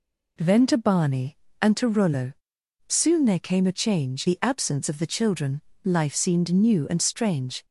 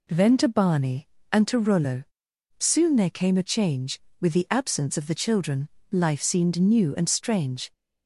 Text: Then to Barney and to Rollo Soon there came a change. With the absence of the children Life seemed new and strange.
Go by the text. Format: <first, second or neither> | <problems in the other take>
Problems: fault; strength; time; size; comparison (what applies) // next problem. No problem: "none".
second | pauses between "Rollo" and "Soon"; noticeable; at 2.3 s; 0.54 s long; noticeable in the second // skips "With"; at 4.2 s // pauses between "children" and "Life"; slight; at 5.6 s; 0.22 s long; slight in the second